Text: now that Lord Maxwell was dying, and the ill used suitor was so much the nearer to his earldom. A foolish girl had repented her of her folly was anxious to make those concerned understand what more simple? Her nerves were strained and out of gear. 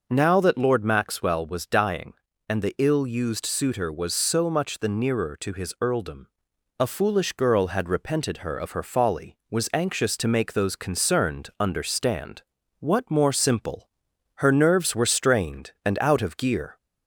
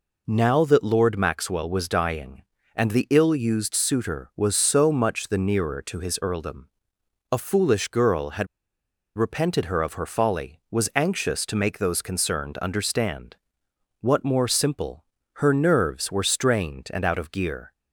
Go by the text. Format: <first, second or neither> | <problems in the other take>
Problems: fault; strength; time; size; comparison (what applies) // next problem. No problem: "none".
first | pauses between "had" and "repented"; noticeable; at 8.4 s; 0.71 s long // pauses between "understand" and "what"; noticeable; at 13.3 s; 0.64 s long; also in the first